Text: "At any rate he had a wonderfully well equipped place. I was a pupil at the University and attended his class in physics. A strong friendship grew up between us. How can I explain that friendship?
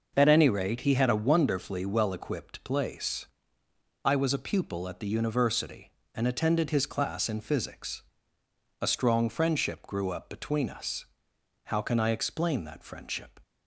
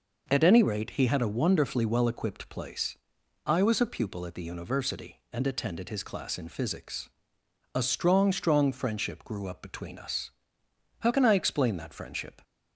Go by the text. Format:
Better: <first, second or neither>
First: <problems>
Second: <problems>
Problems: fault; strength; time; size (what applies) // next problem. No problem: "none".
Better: first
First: none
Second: says "strong" twice; at 8.3 s